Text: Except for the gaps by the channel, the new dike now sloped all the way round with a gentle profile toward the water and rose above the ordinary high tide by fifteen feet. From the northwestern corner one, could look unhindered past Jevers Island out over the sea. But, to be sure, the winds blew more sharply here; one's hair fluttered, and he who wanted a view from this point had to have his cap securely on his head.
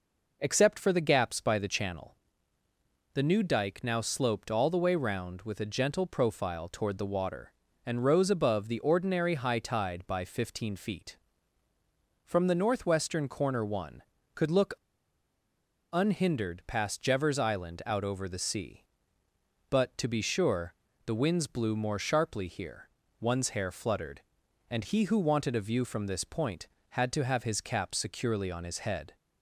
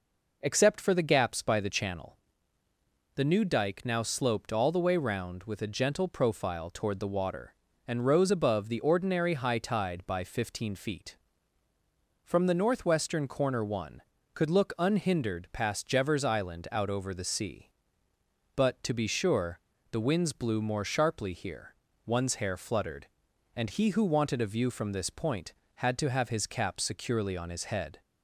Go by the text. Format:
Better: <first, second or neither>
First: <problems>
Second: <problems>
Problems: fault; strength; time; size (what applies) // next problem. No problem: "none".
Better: second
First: pauses between "look" and "unhindered"; at 14.7 s; 1.1 s long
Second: none